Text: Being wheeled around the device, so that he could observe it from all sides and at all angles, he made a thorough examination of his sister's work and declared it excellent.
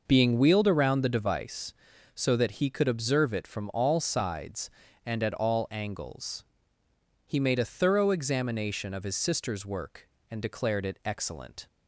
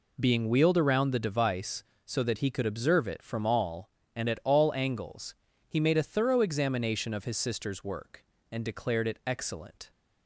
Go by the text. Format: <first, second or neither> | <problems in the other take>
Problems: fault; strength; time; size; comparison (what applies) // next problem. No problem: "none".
first | skips "sides"; at 4.0 s